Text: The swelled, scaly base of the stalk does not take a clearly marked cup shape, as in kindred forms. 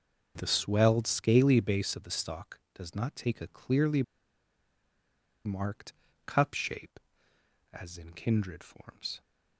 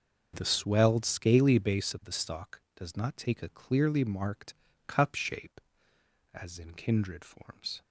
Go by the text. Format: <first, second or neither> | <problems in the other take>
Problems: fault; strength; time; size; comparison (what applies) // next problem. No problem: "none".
second | starts louder than the rest; until 1.3 s; 6.5 dB; also in the second // pauses between "clearly" and "marked"; strong; at 4.0 s; 1.4 s long // pauses between "marked" and "cup"; slight; at 5.9 s; 0.32 s long; slight in the second